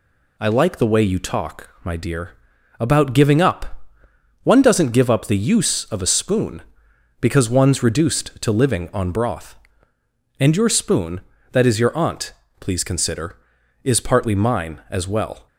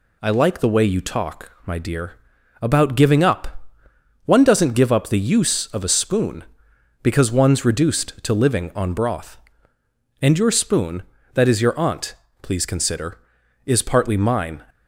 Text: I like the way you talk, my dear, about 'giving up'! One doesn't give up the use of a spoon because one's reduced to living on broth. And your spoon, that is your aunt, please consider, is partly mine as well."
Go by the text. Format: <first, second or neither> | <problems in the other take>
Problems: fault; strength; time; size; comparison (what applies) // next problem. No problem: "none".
first | stops before "as well"; at 14.6 s